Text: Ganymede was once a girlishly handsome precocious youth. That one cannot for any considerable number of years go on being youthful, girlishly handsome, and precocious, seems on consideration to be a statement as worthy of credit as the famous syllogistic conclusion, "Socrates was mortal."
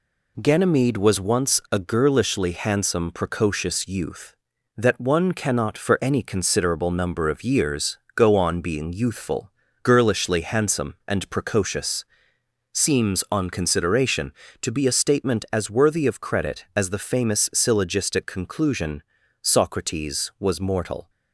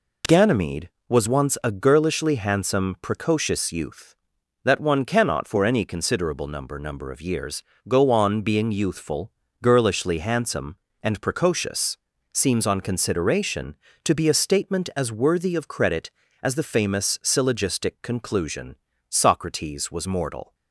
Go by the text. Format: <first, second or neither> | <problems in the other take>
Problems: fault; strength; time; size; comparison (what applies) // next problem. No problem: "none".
first | says "number" twice; at 6.7 s // pauses between "years" and "go"; slight; at 7.6 s; 0.28 s long; slight in the first